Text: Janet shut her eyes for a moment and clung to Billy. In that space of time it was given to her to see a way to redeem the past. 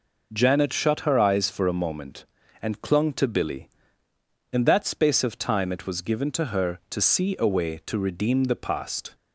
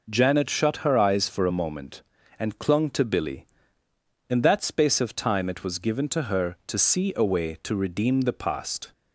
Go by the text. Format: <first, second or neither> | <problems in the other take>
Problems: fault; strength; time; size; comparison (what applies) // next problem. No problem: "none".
neither | none